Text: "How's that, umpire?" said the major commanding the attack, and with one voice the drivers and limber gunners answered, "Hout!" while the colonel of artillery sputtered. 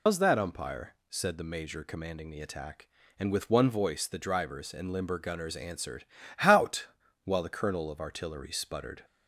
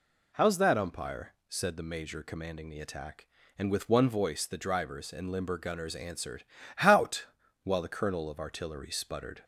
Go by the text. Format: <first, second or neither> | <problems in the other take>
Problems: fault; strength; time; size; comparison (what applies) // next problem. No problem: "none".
second | loses the start of "How's"; at 0.0 s; 105 ms